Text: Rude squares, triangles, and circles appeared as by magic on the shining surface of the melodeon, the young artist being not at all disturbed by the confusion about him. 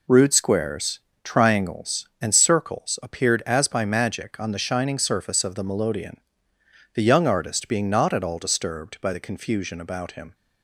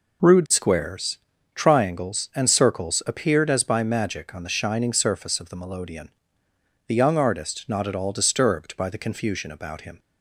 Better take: first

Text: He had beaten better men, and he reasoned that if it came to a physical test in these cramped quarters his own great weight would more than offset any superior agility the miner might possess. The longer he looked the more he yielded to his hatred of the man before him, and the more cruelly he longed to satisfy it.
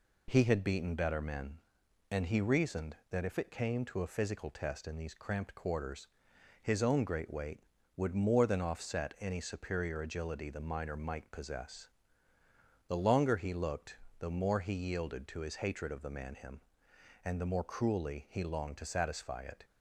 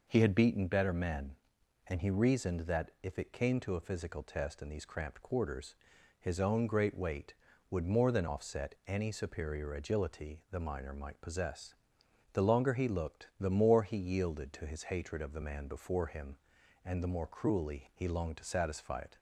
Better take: second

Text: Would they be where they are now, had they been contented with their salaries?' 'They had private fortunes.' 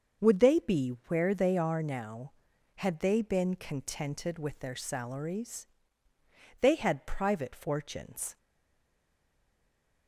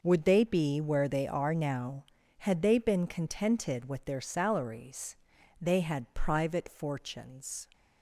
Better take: second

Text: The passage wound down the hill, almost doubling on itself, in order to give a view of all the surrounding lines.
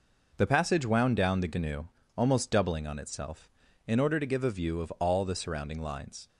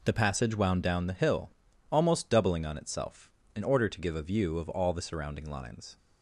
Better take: second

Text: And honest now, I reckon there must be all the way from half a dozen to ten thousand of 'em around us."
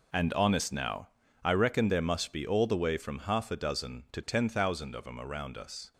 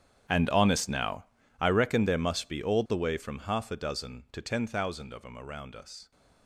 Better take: first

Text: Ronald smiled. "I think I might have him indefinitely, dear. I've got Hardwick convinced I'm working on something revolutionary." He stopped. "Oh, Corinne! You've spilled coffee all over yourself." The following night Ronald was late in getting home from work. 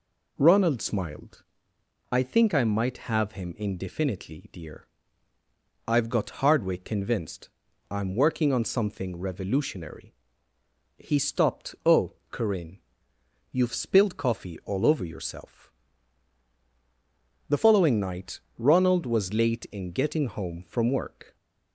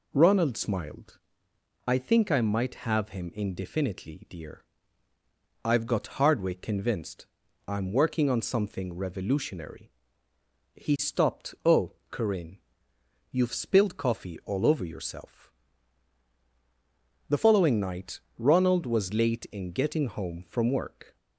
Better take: neither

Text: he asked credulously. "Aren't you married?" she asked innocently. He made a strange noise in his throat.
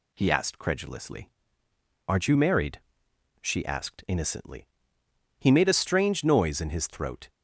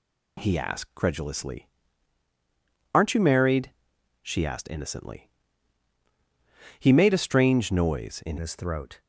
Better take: first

